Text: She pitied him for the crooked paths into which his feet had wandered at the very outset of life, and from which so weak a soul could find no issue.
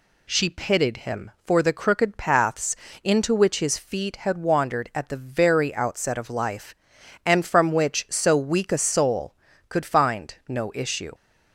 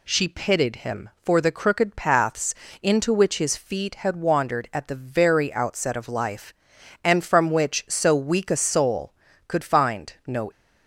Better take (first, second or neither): first